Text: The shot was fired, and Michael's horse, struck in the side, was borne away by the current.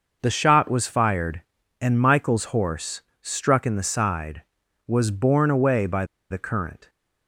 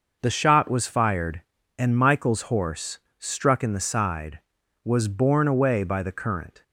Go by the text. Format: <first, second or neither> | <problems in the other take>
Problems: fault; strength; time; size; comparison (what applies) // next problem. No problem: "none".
second | pauses between "by" and "the"; slight; at 6.0 s; 0.26 s long